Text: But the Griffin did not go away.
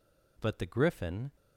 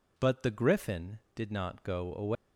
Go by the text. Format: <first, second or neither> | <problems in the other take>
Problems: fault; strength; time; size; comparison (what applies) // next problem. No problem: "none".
second | stops before "did not go away"; at 1.3 s